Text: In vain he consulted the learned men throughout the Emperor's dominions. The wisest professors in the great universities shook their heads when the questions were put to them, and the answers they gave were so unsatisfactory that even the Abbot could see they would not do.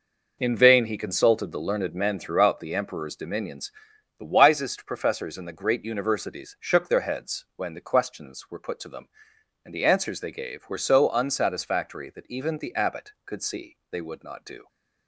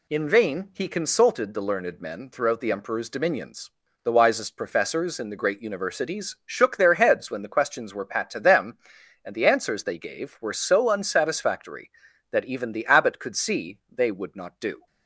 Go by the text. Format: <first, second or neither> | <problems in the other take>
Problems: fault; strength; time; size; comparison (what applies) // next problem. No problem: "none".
first | says "pat" for "put"; at 8.0 s